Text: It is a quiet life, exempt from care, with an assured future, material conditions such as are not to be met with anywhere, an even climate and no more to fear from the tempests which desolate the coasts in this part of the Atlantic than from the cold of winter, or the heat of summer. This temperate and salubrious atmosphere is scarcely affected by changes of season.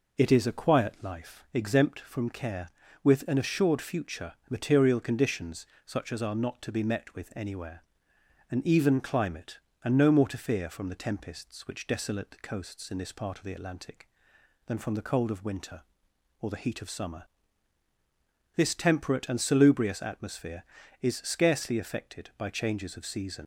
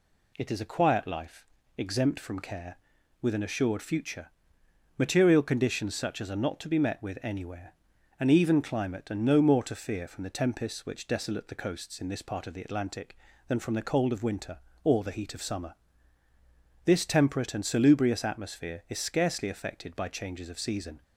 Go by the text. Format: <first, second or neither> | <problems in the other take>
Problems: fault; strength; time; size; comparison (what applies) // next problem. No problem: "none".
second | pauses between "conditions" and "such"; slight; at 5.6 s; 0.22 s long // leaves "season" unfinished; at 23.4 s; 95 ms